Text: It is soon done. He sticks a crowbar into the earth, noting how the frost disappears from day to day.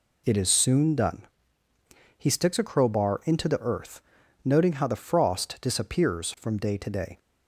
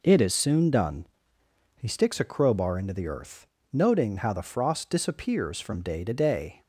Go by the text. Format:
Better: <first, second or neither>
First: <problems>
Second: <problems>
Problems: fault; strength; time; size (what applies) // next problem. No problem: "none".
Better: neither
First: none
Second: none